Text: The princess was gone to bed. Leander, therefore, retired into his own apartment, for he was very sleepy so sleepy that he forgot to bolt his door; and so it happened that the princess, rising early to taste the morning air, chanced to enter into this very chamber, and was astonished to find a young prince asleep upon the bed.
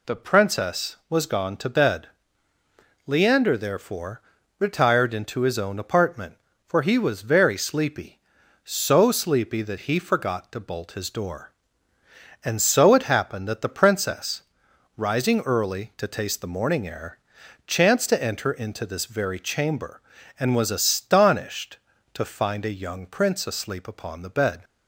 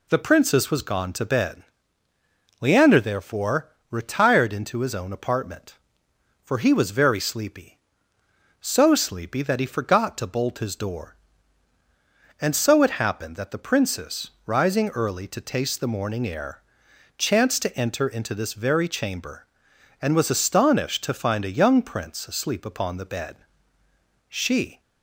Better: first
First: none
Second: goes on to say "She"; from 24.2 s on; 0.50 s long

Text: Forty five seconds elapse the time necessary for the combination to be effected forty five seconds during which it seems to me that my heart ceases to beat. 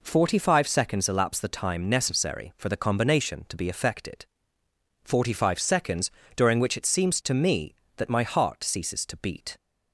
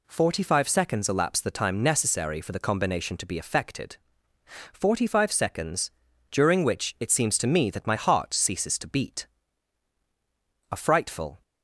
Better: first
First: pauses between "effected" and "forty"; noticeable; at 4.2 s; 0.78 s long // pauses between "seconds" and "during"; slight; at 6.0 s; 0.26 s long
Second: pauses between "effected" and "forty"; noticeable; at 3.9 s; 0.76 s long // pauses between "seconds" and "during"; at 5.8 s; 0.40 s long // goes on to say "A frightful"; noticeable; from 10.7 s on; 0.70 s long

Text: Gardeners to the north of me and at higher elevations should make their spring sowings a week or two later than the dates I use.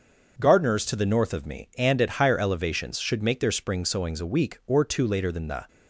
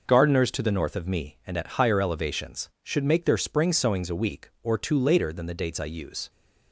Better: second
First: starts louder than the rest; until 1.3 s; 6.5 dB // stops before "dates I use"; at 5.6 s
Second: none

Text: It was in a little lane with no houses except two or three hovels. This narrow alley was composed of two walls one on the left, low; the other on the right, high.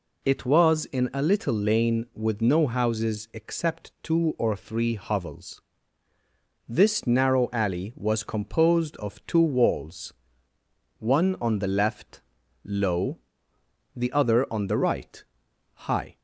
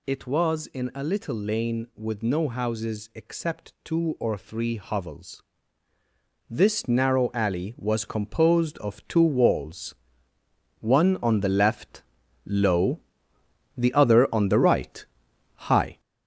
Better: first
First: pauses between "walls" and "one"; noticeable; at 10.1 s; 0.86 s long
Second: gets louder; throughout; 6.5 dB // pauses between "walls" and "one"; noticeable; at 9.9 s; 0.86 s long

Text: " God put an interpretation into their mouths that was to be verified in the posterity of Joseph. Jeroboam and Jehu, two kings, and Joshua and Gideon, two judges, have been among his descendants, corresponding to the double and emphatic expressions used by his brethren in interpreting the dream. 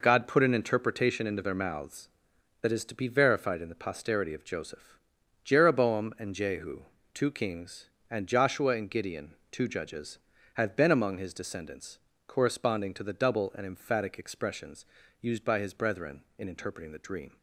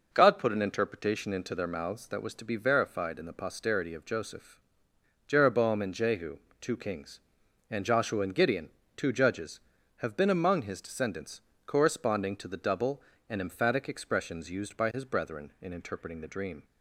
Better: second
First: says "is" for "was"; at 2.7 s // pauses between "expressions" and "used"; slight; at 14.8 s; 0.34 s long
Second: none

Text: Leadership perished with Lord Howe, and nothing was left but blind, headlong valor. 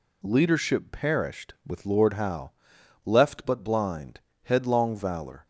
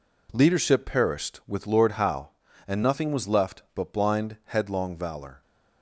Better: second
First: skips "and nothing was"; at 2.7 s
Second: none

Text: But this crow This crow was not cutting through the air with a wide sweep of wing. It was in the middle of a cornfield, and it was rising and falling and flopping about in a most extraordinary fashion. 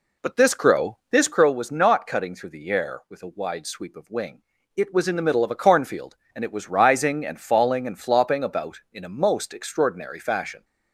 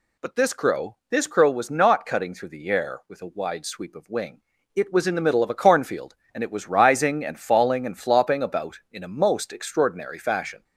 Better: second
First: starts louder than the rest; slight; until 1.4 s; 3 dB // pauses between "crow" and "This"; slight; at 0.9 s; 0.16 s long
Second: pauses between "crow" and "This"; slight; at 0.9 s; 0.16 s long

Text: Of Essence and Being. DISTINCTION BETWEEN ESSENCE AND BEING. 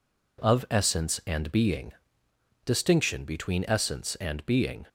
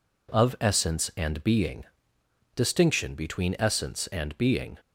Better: neither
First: none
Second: none

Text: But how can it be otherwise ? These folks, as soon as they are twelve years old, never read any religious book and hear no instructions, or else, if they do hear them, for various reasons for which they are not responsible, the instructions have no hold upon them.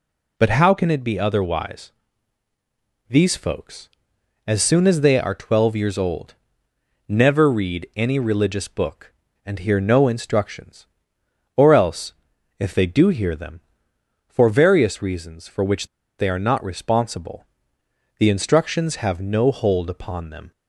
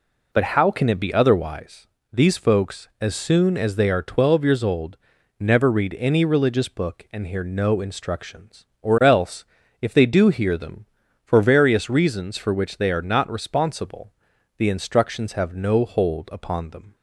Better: second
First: pauses between "which" and "they"; slight; at 15.8 s; 0.32 s long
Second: none

